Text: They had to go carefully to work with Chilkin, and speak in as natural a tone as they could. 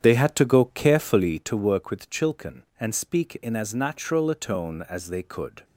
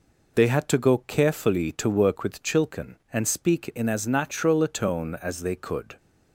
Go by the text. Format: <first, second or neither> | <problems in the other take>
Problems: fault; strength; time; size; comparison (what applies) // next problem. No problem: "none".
second | starts louder than the rest; strong; until 1.4 s; 8.5 dB